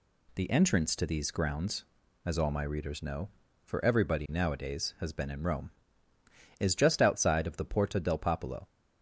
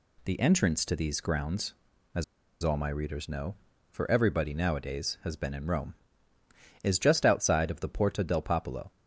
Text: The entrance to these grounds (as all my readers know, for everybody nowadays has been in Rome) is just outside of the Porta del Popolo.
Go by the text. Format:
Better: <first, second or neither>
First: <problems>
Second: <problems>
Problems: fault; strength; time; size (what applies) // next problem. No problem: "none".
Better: first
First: none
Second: pauses between "as" and "all"; at 2.2 s; 0.39 s long